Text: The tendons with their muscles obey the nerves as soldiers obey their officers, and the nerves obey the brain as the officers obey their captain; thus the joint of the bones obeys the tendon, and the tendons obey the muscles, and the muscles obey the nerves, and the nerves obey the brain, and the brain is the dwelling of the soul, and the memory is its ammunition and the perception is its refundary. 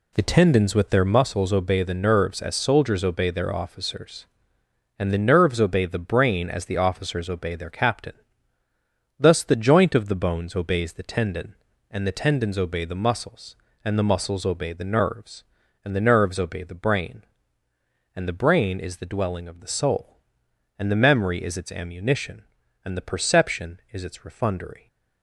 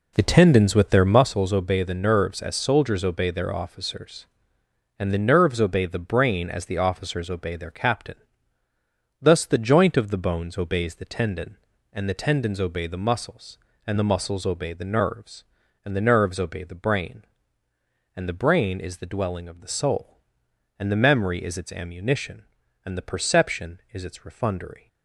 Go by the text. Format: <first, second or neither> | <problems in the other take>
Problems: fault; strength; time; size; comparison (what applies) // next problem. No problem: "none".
first | starts louder than the rest; until 1.5 s; 3.5 dB